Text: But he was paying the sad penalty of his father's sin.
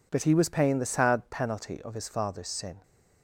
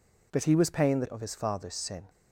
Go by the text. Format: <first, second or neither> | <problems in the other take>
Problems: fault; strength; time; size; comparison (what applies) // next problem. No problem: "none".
first | skips "sad penalty"; at 1.0 s